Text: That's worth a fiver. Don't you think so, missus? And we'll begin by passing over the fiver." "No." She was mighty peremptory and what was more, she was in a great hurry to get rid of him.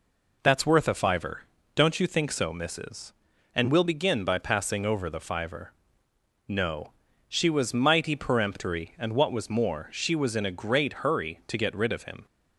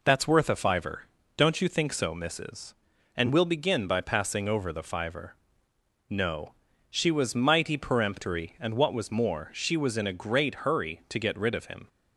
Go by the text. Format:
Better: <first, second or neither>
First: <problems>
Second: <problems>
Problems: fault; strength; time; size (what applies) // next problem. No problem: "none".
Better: neither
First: none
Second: none